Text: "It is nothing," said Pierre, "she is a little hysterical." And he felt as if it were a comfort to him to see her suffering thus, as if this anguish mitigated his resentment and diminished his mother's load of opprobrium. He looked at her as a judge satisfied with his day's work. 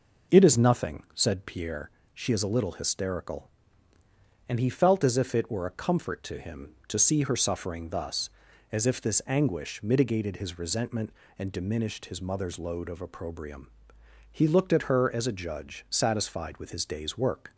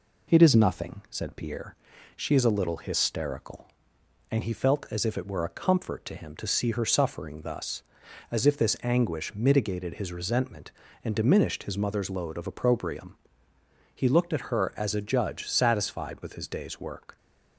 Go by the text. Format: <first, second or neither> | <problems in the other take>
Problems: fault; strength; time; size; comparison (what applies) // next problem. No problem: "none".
neither | none